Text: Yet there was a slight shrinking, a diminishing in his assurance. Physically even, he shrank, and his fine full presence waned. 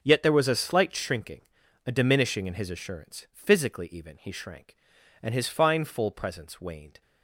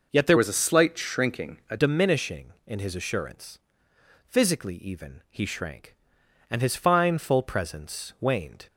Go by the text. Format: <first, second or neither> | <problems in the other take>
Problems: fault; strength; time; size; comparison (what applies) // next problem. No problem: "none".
first | changes voice from "was" to "a"; from 0.3 to 1.7 s; 1.4 s long